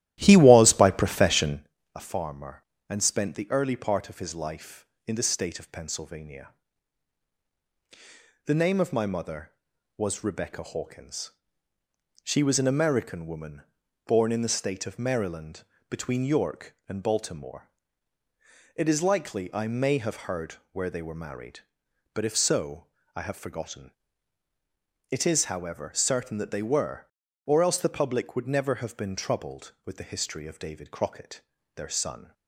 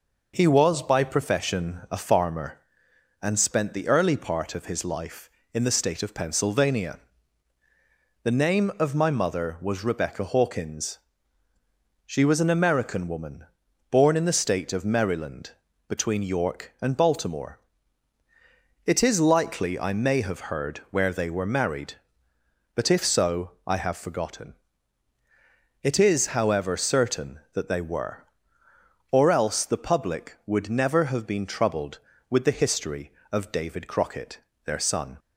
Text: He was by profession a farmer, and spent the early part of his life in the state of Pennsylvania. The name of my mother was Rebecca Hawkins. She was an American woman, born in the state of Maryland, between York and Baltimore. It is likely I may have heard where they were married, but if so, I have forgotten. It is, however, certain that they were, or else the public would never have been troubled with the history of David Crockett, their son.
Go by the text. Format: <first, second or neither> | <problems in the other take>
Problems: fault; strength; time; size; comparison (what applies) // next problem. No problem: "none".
second | starts louder than the rest; strong; until 1.7 s; 13.5 dB // pauses between "profession" and "a"; slight; at 1.6 s; 0.30 s long // pauses between "heard" and "where"; slight; at 20.5 s; 0.18 s long